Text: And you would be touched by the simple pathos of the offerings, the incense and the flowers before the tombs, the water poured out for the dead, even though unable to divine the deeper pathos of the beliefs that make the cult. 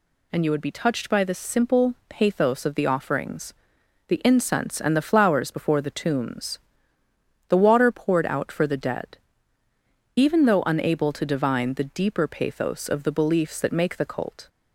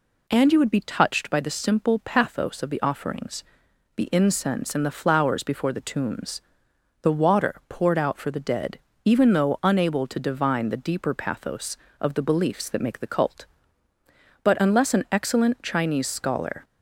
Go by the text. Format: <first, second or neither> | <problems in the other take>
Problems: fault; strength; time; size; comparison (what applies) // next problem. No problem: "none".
first | goes on to say "But unless an excellent Chinese scholar"; strong; from 14.4 s on; 2.2 s long